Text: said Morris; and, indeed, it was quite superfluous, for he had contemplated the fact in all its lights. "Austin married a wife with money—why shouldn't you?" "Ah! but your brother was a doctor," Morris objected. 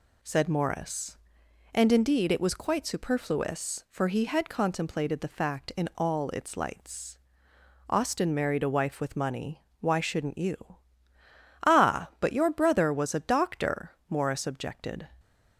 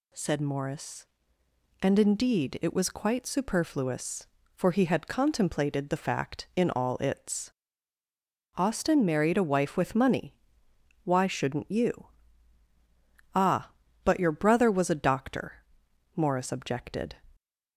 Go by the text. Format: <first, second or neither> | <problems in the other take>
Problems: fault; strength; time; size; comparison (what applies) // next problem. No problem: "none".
first | skips "lights"; at 8.0 s